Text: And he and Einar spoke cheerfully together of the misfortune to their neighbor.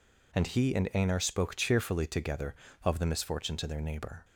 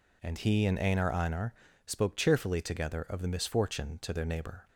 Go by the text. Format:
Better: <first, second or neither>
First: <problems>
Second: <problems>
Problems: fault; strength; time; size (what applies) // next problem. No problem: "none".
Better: first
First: none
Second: says "Einar" twice; at 1.1 s